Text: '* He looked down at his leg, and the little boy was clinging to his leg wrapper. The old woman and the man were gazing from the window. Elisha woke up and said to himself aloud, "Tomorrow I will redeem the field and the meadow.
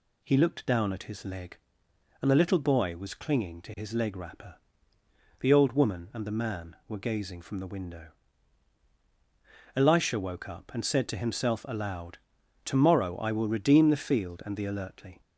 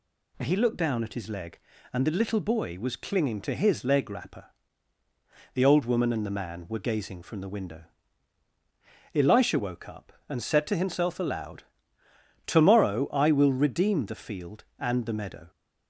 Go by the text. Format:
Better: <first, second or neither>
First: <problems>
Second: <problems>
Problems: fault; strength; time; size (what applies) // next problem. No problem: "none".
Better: second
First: says "alertly" for "meadow"; at 14.6 s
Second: none